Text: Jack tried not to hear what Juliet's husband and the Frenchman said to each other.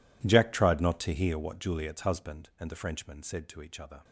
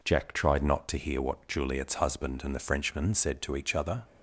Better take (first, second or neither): second